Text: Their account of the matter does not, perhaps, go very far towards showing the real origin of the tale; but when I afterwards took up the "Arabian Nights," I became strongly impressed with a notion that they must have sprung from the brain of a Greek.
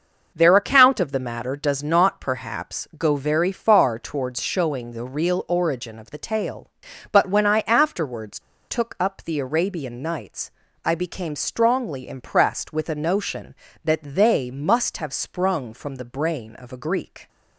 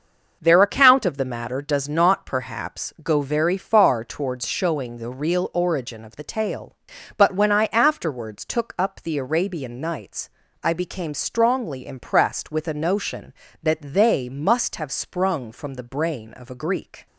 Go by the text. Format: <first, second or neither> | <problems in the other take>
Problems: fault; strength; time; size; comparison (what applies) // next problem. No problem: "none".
second | pauses between "afterwards" and "took"; slight; at 8.3 s; 0.30 s long